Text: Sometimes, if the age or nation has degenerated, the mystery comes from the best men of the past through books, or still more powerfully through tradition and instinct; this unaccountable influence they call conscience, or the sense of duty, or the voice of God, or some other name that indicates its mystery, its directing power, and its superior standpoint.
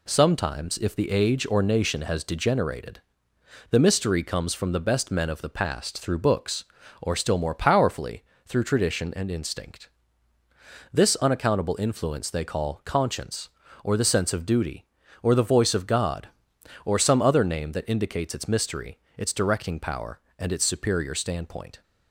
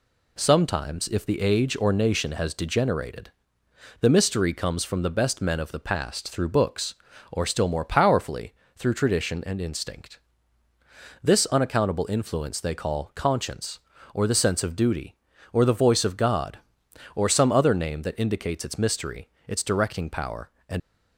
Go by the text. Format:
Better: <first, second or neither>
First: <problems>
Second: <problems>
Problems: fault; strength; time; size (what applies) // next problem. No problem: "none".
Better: first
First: pauses between "powerfully" and "through"; slight; at 8.2 s; 0.22 s long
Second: pauses between "powerfully" and "through"; slight; at 8.5 s; 0.22 s long // stops before "its superior standpoint"; at 20.7 s